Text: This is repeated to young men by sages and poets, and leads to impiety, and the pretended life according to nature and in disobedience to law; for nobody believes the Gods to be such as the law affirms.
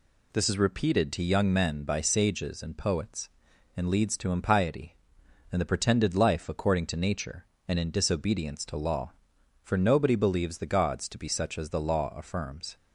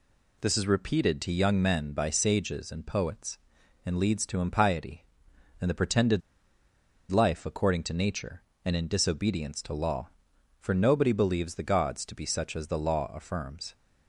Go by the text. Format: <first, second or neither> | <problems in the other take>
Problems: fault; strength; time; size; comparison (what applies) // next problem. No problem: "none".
first | pauses between "pretended" and "life"; noticeable; at 6.2 s; 0.91 s long